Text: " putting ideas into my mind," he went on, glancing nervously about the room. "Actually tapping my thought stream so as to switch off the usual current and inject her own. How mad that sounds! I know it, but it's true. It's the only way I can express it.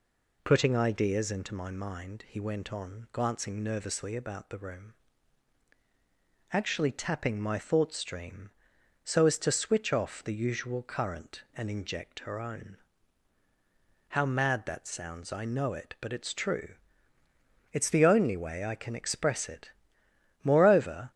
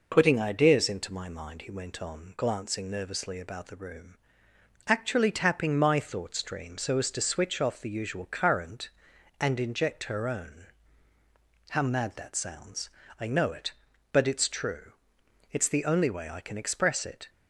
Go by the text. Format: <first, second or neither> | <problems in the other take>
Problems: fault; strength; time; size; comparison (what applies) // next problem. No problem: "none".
second | goes on to say "Moreover"; noticeable; from 20.4 s on; 0.68 s long